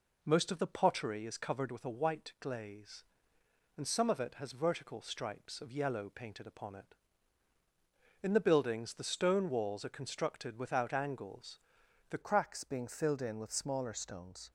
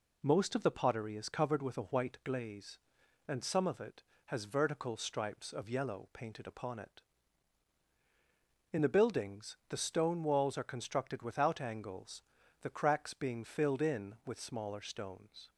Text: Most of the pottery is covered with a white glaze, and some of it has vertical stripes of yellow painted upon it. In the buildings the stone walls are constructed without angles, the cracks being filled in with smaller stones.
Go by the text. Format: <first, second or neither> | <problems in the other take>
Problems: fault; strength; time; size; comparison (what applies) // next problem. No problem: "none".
second | changes voice at "cracks"; from 12.2 s on; 2.3 s long